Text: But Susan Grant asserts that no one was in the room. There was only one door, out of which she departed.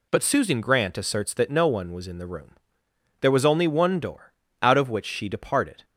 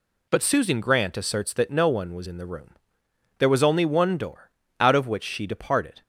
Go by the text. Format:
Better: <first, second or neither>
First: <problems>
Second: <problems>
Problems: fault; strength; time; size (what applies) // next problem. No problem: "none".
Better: neither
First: none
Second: none